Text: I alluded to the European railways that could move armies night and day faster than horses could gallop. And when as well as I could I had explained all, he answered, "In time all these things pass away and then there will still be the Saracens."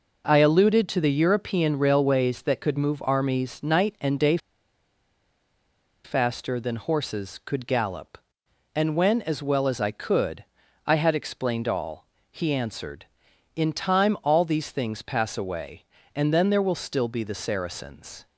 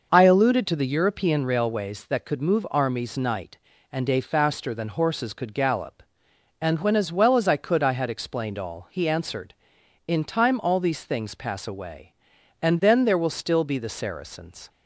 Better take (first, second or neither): second